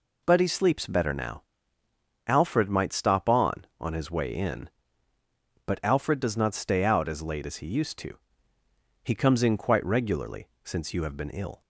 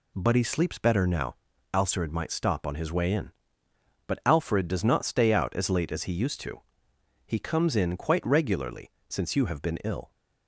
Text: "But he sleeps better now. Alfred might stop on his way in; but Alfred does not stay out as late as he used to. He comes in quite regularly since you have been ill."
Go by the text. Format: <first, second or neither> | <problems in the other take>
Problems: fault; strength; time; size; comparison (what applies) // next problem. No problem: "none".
second | says "on" twice; at 3.7 s // pauses between "regularly" and "since"; slight; at 10.4 s; 0.16 s long; slight in the second